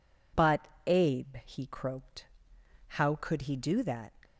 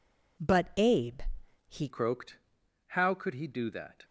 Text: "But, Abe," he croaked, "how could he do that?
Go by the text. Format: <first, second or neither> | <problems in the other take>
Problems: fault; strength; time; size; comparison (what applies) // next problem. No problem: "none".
first | changes voice at "croaked"; from 1.8 s on; 2.2 s long